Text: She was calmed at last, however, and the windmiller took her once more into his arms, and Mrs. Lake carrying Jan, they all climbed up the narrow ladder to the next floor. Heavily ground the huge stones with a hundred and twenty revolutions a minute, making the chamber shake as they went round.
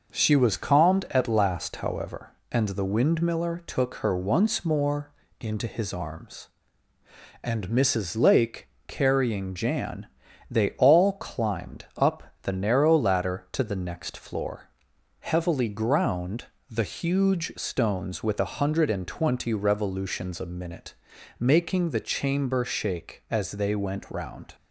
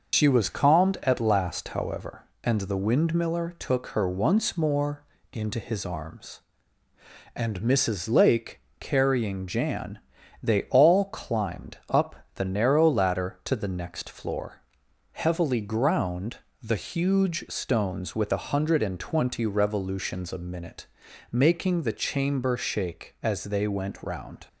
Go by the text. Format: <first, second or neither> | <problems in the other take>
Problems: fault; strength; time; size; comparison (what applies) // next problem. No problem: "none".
first | loses the start of "She"; at 0.1 s; 110 ms // starts louder than the rest; noticeable; until 1.1 s; 6 dB // pauses between "more" and "into"; slight; at 5.0 s; 0.28 s long; slight in the first // pauses between "Lake" and "carrying"; slight; at 8.5 s; 0.22 s long; slight in the first // pauses between "up" and "the"; slight; at 12.1 s; 0.20 s long; slight in the first // pauses between "ground" and "the"; slight; at 16.3 s; 0.24 s long; slight in the first